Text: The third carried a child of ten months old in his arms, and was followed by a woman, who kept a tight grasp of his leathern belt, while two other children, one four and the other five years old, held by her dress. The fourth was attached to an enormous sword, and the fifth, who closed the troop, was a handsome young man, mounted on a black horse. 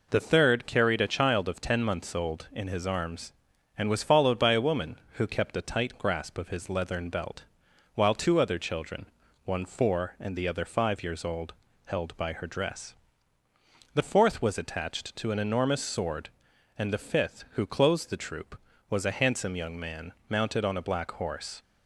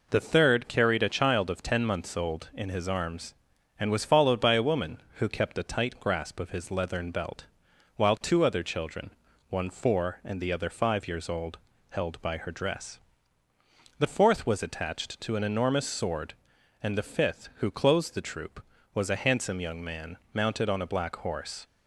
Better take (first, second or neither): neither